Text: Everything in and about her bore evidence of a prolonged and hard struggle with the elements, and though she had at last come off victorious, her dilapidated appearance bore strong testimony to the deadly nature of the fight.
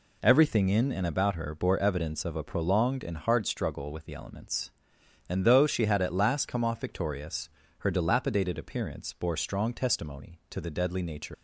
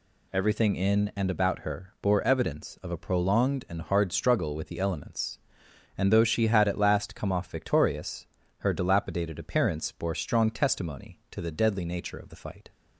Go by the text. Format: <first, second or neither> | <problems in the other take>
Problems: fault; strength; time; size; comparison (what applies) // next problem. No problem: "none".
second | stops before "of the fight"; at 11.3 s